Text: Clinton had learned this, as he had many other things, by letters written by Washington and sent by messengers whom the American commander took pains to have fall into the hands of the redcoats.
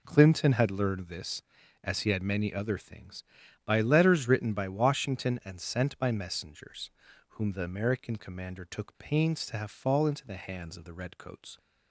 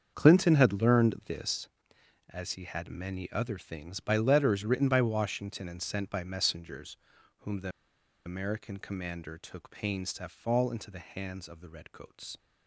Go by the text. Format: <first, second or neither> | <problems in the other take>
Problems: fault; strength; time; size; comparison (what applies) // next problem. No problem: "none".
first | starts louder than the rest; until 1.1 s; 7 dB // pauses between "messengers" and "whom"; at 6.9 s; 0.42 s long; also in the first // pauses between "the" and "American"; noticeable; at 7.6 s; 0.56 s long